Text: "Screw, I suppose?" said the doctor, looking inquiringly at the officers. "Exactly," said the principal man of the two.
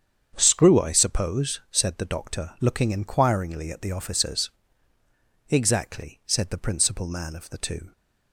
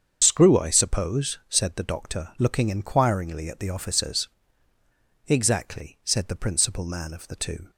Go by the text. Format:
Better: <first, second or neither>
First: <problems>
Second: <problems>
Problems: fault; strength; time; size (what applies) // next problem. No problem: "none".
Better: first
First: starts louder than the rest; strong; until 1.3 s; 7.5 dB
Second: loses the start of "Screw"; at 0.2 s; 105 ms // starts louder than the rest; strong; until 1.2 s; 7 dB